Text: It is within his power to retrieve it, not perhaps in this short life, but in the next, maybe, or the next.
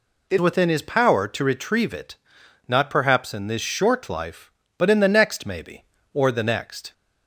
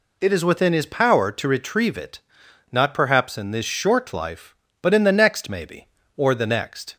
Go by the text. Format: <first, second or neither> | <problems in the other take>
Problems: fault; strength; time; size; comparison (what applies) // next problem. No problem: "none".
second | skips "is"; at 0.3 s